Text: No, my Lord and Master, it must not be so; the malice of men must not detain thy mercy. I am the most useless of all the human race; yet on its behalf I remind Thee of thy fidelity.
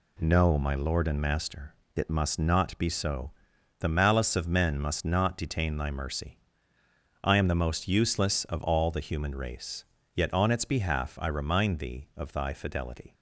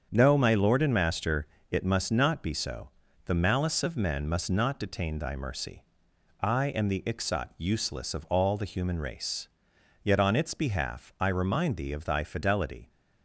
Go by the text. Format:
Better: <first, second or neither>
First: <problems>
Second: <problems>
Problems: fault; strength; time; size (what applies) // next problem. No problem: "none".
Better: first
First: none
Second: starts louder than the rest; strong; until 1.1 s; 7 dB // says "ixot" for "most"; at 7.0 s